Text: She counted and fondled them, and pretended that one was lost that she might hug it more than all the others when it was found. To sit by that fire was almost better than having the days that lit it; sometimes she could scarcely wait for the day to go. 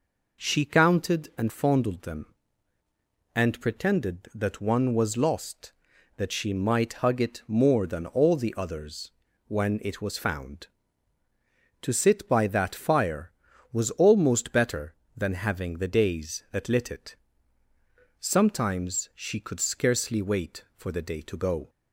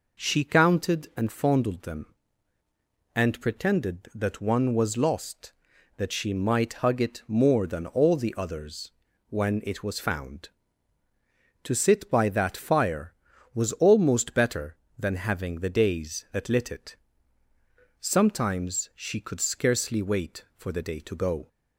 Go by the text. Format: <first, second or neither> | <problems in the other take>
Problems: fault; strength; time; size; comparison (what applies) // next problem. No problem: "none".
neither | pauses between "others" and "when"; the same in both